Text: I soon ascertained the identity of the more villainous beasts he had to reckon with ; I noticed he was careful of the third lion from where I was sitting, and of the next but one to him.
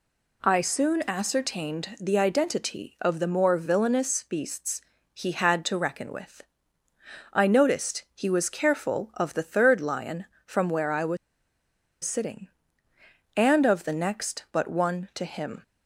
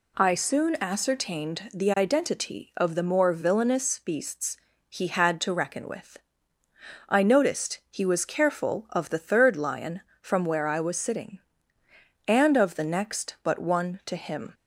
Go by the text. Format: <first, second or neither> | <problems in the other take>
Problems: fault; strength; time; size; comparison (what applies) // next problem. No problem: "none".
second | pauses between "beasts" and "he"; slight; at 4.7 s; 0.32 s long; slight in the second // pauses between "was" and "sitting"; noticeable; at 11.1 s; 0.87 s long